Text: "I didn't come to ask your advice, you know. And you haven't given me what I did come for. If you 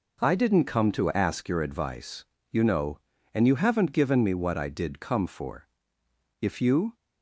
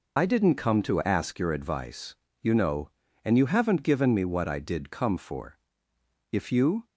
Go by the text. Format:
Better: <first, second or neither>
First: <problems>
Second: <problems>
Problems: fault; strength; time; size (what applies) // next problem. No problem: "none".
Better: first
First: none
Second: loses the start of "I"; at 0.1 s; 65 ms